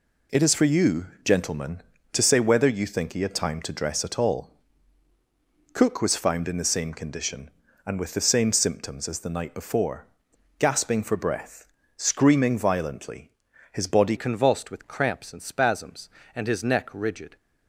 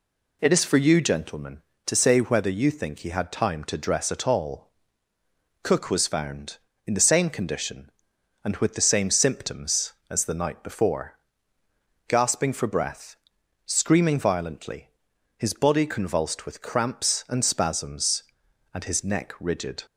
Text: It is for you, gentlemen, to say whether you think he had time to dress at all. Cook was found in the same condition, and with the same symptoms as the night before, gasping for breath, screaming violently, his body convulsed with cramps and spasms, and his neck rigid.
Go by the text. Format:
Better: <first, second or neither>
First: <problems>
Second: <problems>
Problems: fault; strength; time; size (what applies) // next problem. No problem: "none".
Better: second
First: changes voice at "convulsed"; from 14.1 s on; 3.2 s long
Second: none